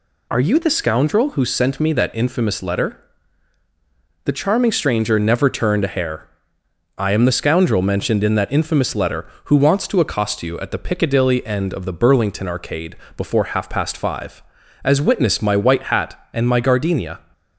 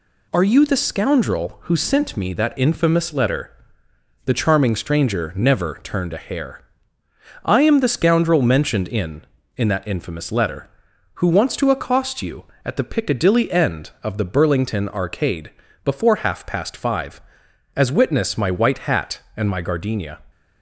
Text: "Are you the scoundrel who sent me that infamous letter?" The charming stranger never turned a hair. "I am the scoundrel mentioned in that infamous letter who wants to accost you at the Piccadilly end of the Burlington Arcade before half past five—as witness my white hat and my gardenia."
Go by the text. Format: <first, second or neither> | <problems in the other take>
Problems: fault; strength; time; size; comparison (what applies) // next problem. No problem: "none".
first | says "in" twice; at 9.5 s // pauses between "Arcade" and "before"; slight; at 15.5 s; 0.32 s long; slight in the first